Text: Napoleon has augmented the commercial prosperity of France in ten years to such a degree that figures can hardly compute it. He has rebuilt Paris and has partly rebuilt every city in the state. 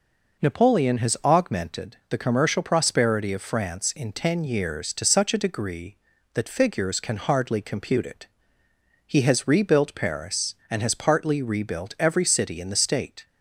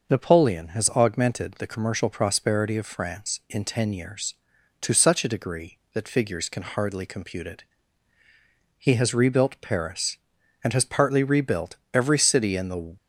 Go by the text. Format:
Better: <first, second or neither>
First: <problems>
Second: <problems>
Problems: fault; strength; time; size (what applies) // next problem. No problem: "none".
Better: first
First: none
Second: stops before "state"; at 12.9 s